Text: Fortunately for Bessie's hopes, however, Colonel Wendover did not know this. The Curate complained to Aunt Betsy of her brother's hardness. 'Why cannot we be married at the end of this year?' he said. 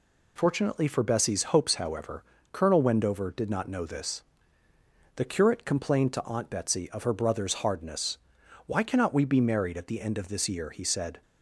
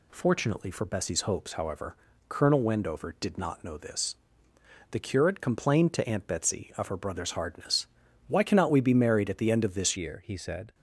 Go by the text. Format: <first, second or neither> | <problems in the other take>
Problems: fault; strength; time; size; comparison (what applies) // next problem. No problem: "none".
first | changes voice at "year"; from 9.9 s on; 0.8 s long